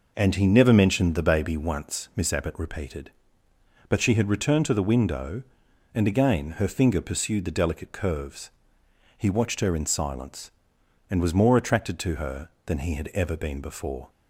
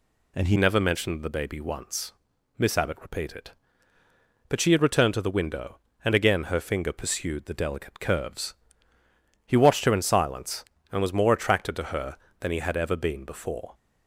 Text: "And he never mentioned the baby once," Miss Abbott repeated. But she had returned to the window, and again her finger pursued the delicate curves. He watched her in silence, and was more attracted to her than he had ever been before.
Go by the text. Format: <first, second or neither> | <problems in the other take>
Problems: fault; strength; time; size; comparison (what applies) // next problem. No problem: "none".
first | changes voice at "never"; from 0.5 s on; 13.2 s long